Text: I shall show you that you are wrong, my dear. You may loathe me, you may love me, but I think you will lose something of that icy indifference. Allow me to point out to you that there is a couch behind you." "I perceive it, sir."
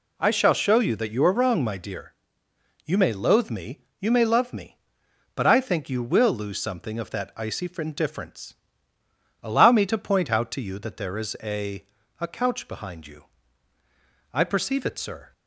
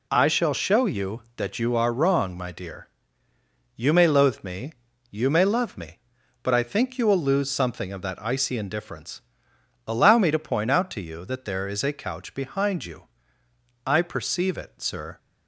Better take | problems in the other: second | says "a" twice; at 12.1 s

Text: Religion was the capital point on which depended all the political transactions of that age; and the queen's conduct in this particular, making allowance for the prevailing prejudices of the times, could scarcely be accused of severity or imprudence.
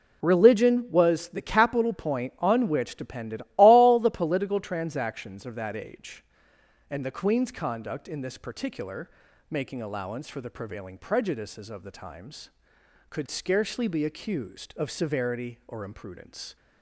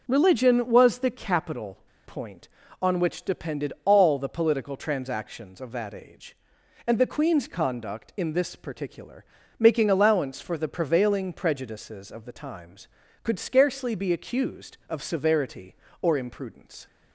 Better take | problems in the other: first | pauses between "capital" and "point"; slight; at 1.7 s; 0.29 s long

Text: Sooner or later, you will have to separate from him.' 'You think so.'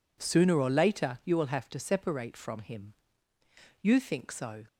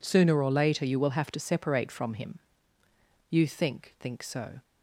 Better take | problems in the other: first | says "think" twice; at 3.9 s

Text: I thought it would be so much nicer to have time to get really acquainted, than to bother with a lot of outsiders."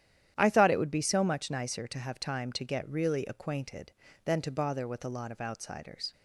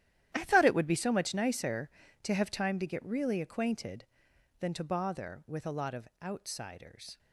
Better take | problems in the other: first | gets quieter; strong; throughout; 15 dB // starts louder than the rest; strong; until 1.3 s; 11.5 dB; strong in the first // pauses between "of" and "outsiders"; slight; at 6.0 s; 0.16 s long

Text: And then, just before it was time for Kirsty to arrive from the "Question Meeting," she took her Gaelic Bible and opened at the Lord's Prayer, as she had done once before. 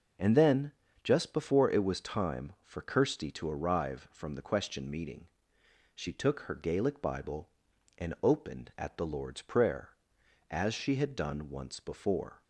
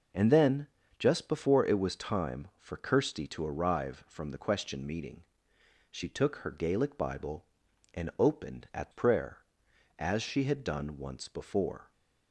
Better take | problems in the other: first | skips "the Lord's"; at 8.9 s

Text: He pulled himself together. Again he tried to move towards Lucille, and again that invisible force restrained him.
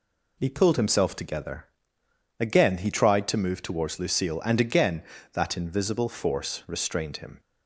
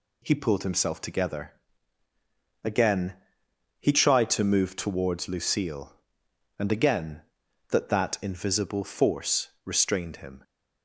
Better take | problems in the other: first | pauses between "Again" and "he"; noticeable; at 3.1 s; 0.66 s long // says "that" twice; at 7.8 s

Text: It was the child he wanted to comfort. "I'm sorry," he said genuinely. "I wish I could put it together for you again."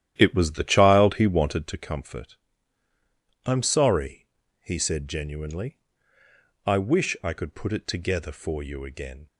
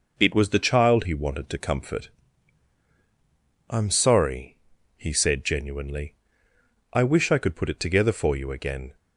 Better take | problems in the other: second | starts louder than the rest; strong; until 1.7 s; 11 dB

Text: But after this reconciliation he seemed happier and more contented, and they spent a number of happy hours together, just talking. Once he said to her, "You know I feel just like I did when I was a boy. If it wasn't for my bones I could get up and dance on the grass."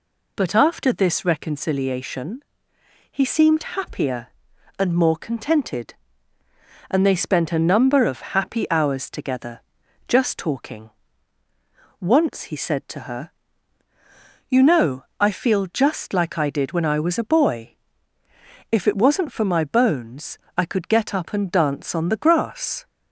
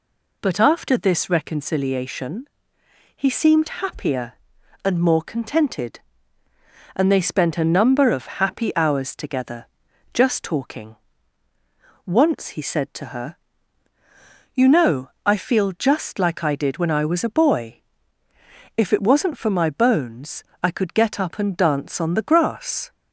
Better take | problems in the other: neither | pauses between "reconciliation" and "he"; noticeable; the same in both // pauses between "know" and "I"; slight; the same in both // pauses between "bones" and "I"; slight; the same in both

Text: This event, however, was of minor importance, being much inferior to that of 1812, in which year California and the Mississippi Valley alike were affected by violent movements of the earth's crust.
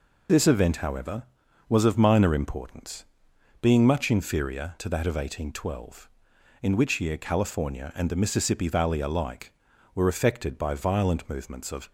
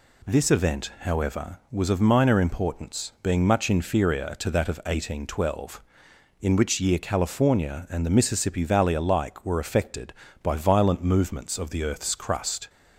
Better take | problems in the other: second | stops before "the earth's crust"; at 11.8 s

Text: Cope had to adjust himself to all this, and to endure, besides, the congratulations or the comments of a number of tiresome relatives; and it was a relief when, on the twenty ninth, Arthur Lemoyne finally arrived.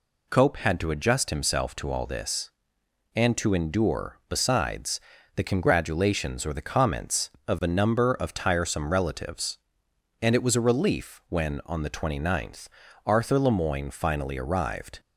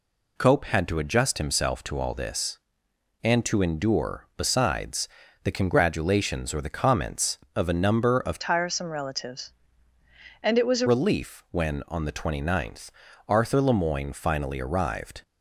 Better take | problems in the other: first | changes voice from "tiresome" to "a"; from 8.4 to 10.8 s; 2.4 s long

